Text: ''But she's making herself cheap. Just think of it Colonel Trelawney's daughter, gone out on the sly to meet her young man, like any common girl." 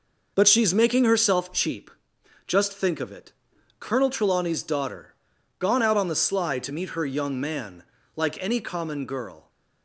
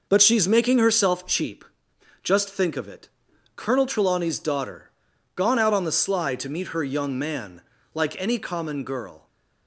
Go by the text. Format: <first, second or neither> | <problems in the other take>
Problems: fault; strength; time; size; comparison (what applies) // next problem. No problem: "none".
neither | pauses between "it" and "Colonel"; noticeable; the same in both